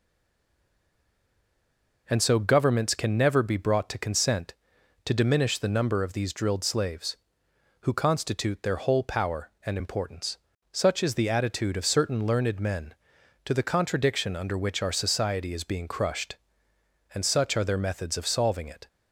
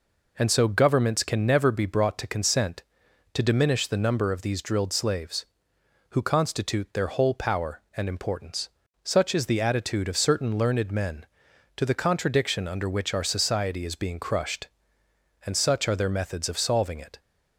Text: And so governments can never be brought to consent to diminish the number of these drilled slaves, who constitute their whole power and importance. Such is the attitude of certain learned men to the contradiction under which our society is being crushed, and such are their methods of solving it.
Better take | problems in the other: second | stays silent before the first word; noticeable; until 2.0 s; 2.0 s long

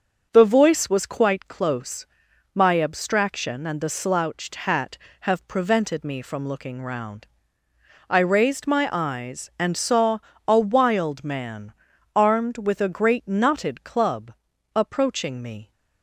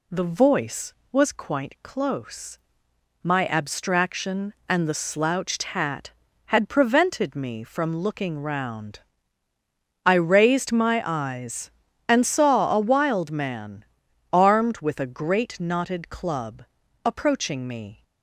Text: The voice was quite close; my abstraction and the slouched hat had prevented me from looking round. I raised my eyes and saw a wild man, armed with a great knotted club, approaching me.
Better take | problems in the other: second | starts louder than the rest; until 1.3 s; 6.5 dB // says "have" for "had"; at 5.2 s // pauses between "saw" and "a"; slight; at 10.1 s; 0.28 s long

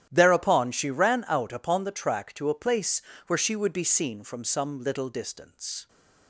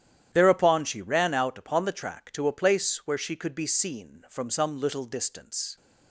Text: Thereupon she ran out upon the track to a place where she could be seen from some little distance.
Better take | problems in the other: second | starts louder than the rest; strong; until 1.1 s; 11 dB; strong in the second // pauses between "place" and "where"; slight; at 3.0 s; 0.24 s long // says "would" for "could"; at 3.5 s

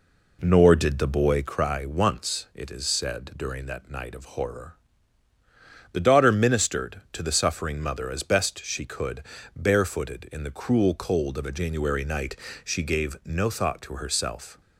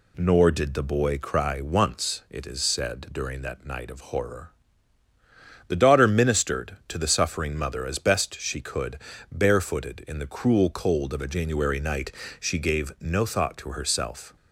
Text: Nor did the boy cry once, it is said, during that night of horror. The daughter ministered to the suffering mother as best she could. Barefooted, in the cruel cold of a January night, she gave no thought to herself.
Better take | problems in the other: second | starts louder than the rest; slight; until 1.6 s; 3 dB

